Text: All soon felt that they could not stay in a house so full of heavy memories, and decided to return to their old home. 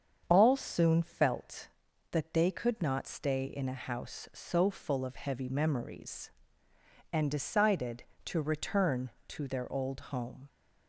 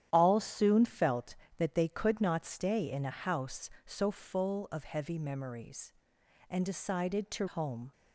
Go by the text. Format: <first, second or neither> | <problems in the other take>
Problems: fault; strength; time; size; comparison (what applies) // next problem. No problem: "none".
first | starts louder than the rest; strong; until 1.1 s; 11 dB; strong in the first // skips "return to their old"; at 7.4 s